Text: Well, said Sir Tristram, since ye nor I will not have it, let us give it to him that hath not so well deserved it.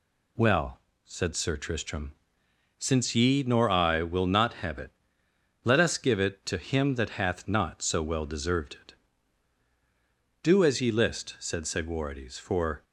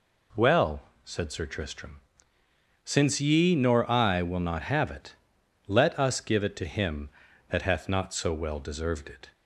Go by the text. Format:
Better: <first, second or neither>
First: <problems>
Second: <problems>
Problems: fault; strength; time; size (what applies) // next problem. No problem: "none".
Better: second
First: goes on to say "Do as ye list said Segwarides for"; strong; from 10.4 s on; 2.4 s long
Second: none